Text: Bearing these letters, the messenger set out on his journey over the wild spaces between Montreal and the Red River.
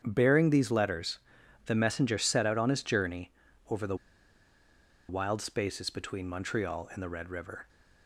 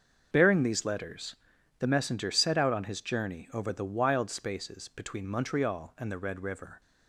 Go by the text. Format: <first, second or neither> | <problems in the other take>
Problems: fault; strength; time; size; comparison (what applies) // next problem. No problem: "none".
second | starts louder than the rest; strong; until 1.0 s; 8 dB; also in the second // pauses between "journey" and "over"; at 3.3 s; 0.38 s long // pauses between "the" and "wild"; at 3.9 s; 1.1 s long